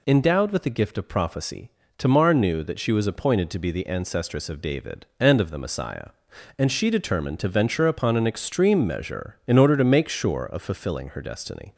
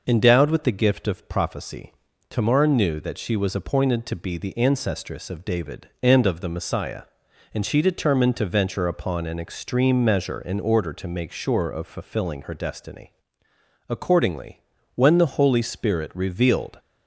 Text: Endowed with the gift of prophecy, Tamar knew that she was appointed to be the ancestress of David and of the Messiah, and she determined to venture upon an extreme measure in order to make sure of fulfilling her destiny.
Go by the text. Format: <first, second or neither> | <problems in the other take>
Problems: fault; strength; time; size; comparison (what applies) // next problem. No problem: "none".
first | goes on to say "Accordingly when the holy spirit revealed"; strong; from 13.8 s on; 2.9 s long